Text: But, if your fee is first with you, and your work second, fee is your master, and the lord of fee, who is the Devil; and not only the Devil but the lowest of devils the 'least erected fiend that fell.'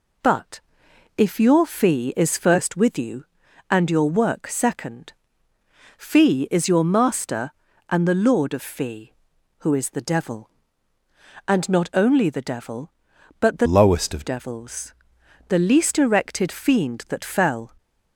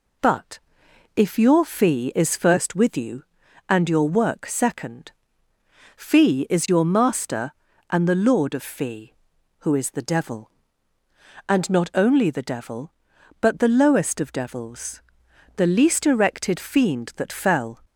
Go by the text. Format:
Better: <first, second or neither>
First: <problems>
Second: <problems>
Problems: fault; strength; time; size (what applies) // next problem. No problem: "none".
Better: second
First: changes voice from "lowest" to "of"; from 13.6 to 14.2 s; 0.6 s long // pauses between "devils" and "the"; noticeable; at 14.9 s; 0.56 s long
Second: pauses between "devils" and "the"; noticeable; at 15.0 s; 0.56 s long